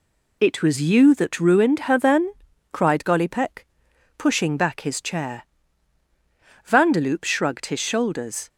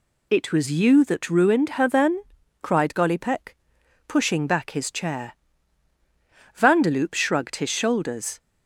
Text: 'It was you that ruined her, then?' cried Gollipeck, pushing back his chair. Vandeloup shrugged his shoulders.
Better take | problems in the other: second | gets quieter; noticeable; throughout; 4.5 dB

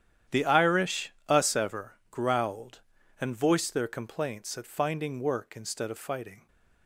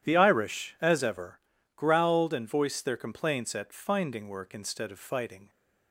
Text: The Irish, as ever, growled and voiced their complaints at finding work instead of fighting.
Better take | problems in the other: second | starts louder than the rest; strong; until 1.4 s; 10.5 dB; strong in the second // says "us" for "as"; at 1.2 s

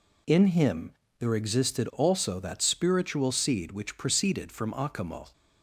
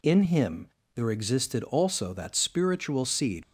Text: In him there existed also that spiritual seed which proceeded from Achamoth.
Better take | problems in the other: first | pauses between "him" and "there"; slight; at 0.6 s; 0.26 s long; slight in the first // stops before "which proceeded from Achamoth"; at 3.4 s

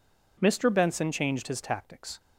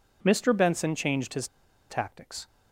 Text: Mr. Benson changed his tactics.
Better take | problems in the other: first | pauses between "his" and "tactics"; at 1.4 s; 0.41 s long

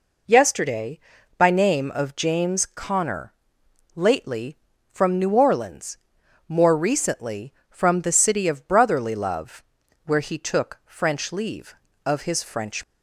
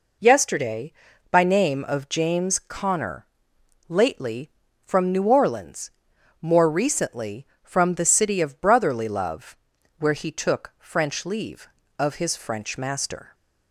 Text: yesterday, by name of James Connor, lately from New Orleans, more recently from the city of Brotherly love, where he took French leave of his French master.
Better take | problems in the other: second | stops before "master"; at 12.8 s

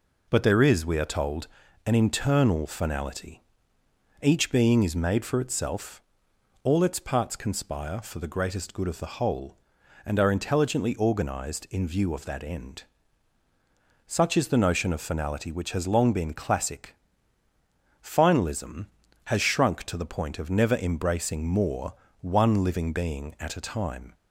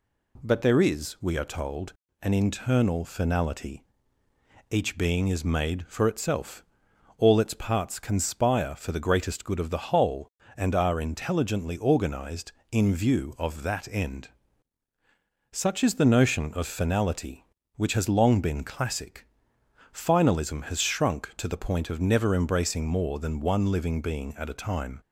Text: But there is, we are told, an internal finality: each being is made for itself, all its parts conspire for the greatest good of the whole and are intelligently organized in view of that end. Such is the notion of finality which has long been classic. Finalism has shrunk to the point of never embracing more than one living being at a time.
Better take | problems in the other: second | skips "than"; at 22.0 s

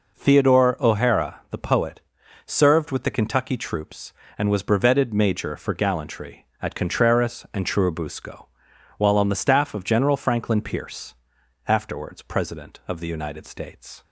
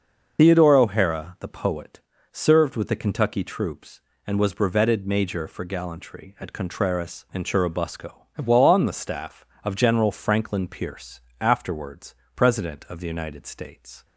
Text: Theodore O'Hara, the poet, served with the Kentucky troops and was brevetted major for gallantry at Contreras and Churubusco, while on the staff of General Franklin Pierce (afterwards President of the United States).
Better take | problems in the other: first | loses the start of "Theodore"; at 0.3 s; 115 ms // starts louder than the rest; noticeable; until 1.4 s; 6 dB // pauses between "afterwards" and "President"; slight; at 12.1 s; 0.22 s long

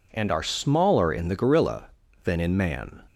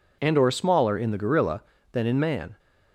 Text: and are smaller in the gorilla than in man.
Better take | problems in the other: first | says "or" for "are"; at 0.3 s

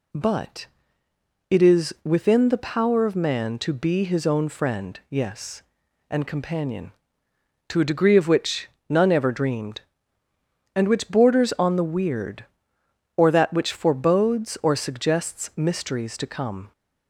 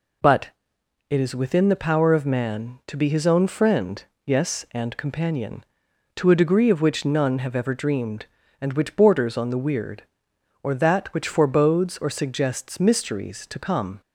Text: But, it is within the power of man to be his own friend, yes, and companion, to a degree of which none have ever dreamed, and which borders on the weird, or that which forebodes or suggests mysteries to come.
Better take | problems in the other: second | pauses between "which" and "none"; slight; at 8.6 s; 0.22 s long // skips "have"; at 9.1 s

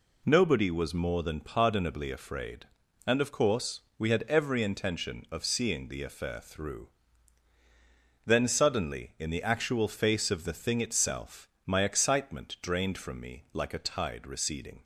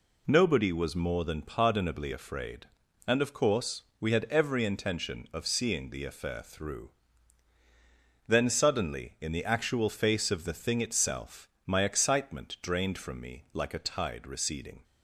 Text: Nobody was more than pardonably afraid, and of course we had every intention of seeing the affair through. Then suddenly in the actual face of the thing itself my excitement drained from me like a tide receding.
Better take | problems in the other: neither | pauses between "course" and "we"; slight; the same in both // pauses between "itself" and "my"; slight; the same in both

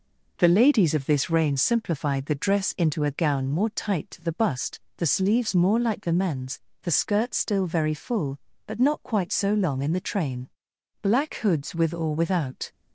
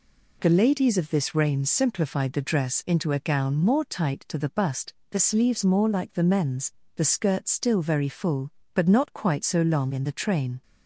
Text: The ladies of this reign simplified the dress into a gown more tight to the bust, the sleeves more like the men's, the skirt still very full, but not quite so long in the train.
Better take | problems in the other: second | goes on to say "Black hoods with or without"; strong; from 11.0 s on; 1.7 s long

